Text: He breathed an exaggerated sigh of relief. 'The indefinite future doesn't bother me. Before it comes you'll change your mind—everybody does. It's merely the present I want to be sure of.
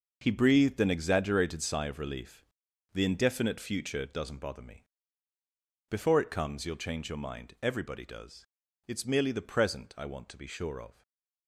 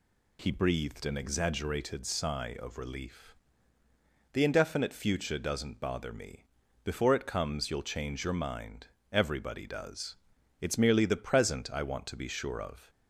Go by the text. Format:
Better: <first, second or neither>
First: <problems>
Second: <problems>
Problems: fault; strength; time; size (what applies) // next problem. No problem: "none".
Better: second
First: gets quieter; strong; throughout; 11 dB // stays silent after the last word; slight; from 10.9 s on; 0.5 s long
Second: none